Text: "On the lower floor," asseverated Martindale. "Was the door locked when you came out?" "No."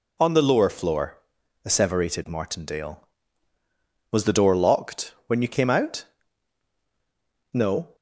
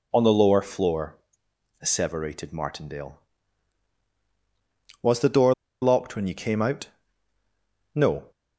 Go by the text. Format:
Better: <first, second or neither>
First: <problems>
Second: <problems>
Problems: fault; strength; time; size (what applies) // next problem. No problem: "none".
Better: first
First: none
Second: pauses between "door" and "locked"; slight; at 5.5 s; 0.29 s long